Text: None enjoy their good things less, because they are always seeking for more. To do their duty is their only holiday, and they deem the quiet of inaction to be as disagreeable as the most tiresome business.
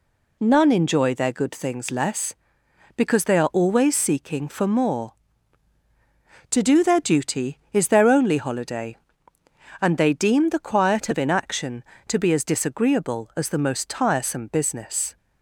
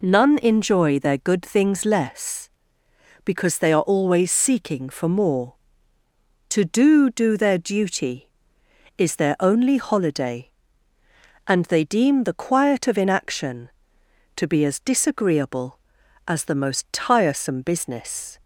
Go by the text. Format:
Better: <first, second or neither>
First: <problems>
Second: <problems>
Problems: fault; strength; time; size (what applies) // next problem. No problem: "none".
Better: first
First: none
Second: says "do" twice; at 7.1 s